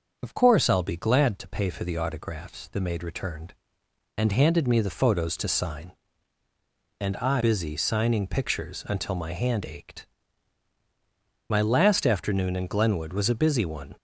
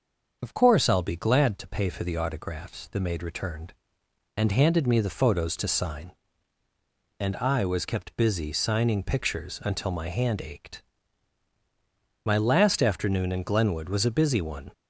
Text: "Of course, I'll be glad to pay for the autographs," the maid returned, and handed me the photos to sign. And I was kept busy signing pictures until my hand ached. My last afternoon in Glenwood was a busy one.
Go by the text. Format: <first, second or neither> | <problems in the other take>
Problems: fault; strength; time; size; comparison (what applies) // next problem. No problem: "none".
second | starts louder than the rest; until 1.2 s; 6.5 dB; also in the second // skips "was kept"; at 7.4 s